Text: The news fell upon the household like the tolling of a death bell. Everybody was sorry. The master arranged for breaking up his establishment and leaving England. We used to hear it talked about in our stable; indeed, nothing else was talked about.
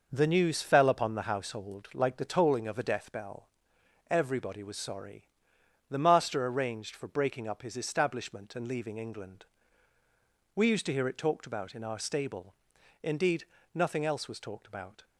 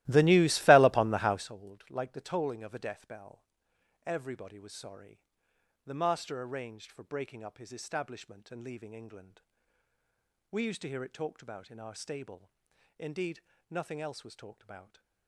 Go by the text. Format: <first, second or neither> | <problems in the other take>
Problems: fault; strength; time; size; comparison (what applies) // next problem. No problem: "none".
first | starts louder than the rest; strong; until 1.5 s; 16.5 dB